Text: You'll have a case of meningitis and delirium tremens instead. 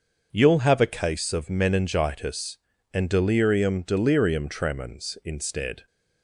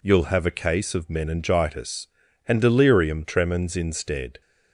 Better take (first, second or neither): second